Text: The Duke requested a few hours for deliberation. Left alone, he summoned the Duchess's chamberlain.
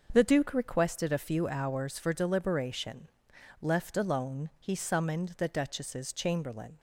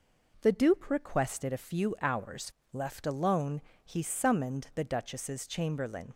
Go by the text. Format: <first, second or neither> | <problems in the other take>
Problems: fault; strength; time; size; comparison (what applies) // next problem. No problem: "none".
first | skips "for deliberation"; at 2.6 s